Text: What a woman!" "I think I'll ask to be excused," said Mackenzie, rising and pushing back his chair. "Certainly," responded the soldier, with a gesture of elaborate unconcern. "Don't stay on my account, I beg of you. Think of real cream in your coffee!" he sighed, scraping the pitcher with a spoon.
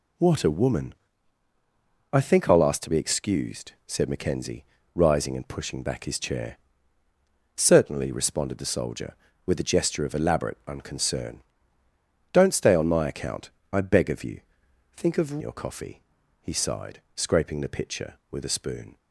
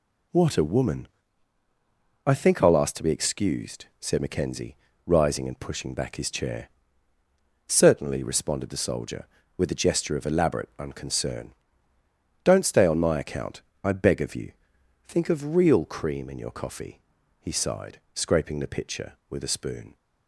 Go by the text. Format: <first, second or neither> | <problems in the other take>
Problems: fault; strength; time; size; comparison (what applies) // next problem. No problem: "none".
second | skips "real cream in"; at 15.4 s